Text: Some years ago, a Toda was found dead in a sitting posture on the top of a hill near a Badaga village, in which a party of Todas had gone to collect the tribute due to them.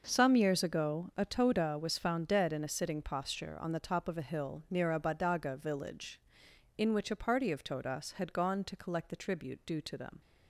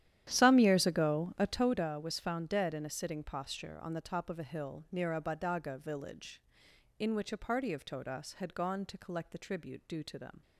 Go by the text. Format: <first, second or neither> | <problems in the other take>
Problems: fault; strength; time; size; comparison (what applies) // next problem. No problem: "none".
first | starts louder than the rest; strong; until 1.7 s; 11.5 dB